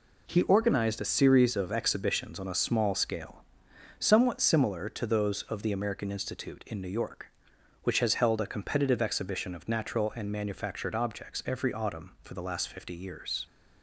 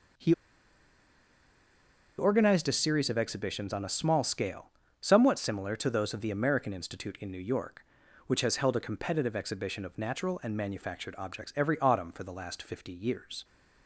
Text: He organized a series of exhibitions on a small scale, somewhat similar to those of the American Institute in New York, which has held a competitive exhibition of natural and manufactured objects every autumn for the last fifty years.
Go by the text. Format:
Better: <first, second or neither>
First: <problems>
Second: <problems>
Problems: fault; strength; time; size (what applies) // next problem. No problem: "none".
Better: first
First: none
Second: pauses between "He" and "organized"; strong; at 0.3 s; 1.8 s long